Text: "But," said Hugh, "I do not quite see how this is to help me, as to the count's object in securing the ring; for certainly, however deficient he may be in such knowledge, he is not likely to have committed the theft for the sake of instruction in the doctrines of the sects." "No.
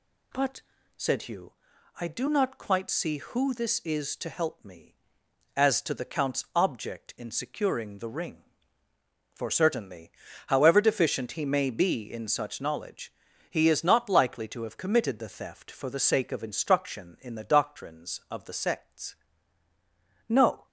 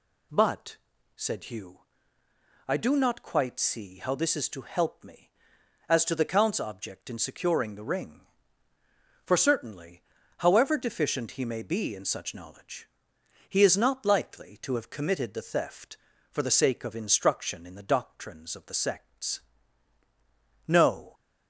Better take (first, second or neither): second